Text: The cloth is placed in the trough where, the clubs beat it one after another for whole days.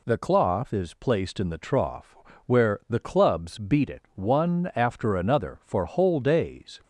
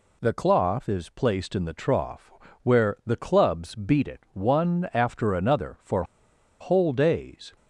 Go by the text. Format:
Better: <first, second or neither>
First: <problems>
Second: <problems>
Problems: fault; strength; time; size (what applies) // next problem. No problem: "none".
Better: first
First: pauses between "trough" and "where"; slight; at 2.1 s; 0.30 s long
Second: pauses between "trough" and "where"; slight; at 2.3 s; 0.32 s long // pauses between "for" and "whole"; noticeable; at 6.0 s; 0.57 s long